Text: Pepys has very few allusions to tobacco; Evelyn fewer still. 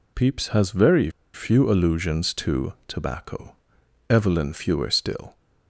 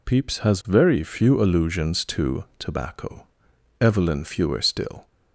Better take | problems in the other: second | pauses between "very" and "few"; slight; at 1.0 s; 0.24 s long

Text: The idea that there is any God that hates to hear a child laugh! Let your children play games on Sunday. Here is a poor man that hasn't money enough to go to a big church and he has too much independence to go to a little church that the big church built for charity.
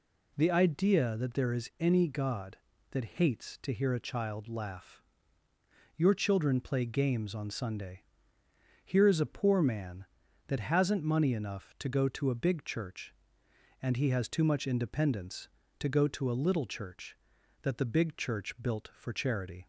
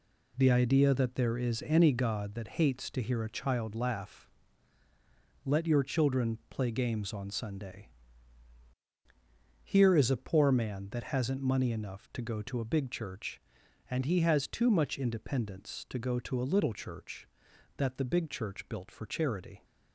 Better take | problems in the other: second | skips "Let"; at 5.4 s

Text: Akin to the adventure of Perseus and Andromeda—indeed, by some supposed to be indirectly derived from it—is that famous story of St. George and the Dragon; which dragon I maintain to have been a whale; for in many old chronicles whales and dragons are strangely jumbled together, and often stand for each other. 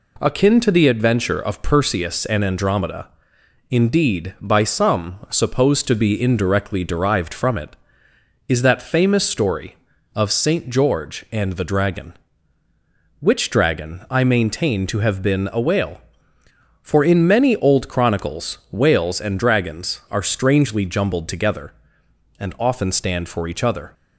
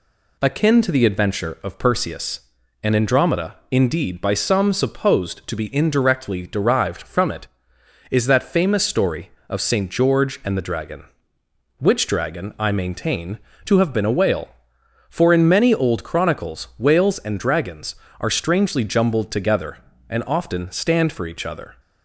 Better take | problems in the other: neither | none

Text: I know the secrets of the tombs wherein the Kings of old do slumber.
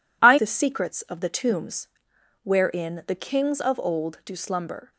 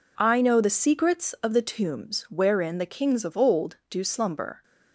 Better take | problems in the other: second | skips "know"; at 0.3 s // pauses between "tombs" and "wherein"; noticeable; at 1.8 s; 0.56 s long

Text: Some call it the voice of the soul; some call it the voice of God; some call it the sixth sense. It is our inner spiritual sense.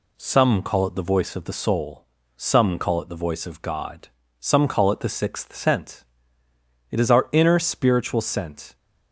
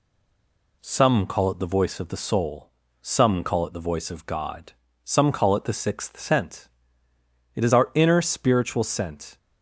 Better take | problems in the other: first | stays silent before the first word; slight; until 0.7 s; 0.7 s long

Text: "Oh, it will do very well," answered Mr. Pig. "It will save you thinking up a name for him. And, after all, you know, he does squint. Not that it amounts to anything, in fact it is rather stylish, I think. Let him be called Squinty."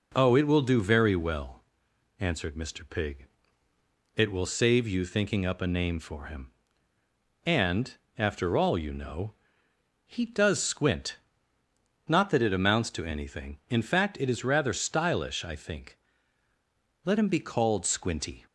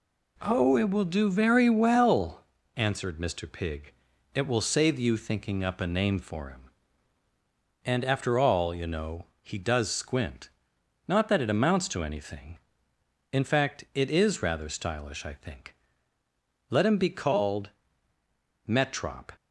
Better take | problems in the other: first | says "Metrop" for "Squinty"; at 18.6 s

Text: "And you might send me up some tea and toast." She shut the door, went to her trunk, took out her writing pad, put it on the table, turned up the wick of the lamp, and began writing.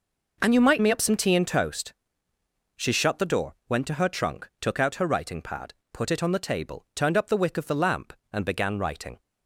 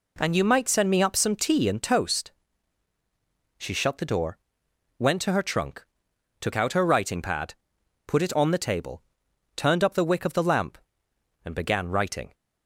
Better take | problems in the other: second | skips "send"; at 0.8 s

